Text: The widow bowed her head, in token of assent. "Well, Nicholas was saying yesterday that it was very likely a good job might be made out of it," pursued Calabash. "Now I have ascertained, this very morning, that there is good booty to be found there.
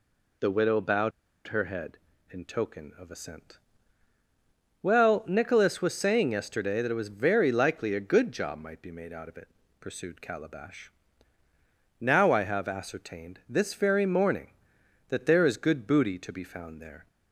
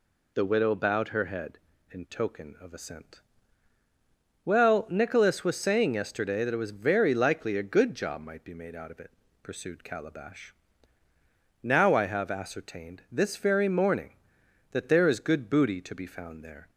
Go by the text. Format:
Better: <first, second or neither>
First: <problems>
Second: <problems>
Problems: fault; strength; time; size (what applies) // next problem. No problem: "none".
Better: second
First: pauses between "bowed" and "her"; at 1.1 s; 0.37 s long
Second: none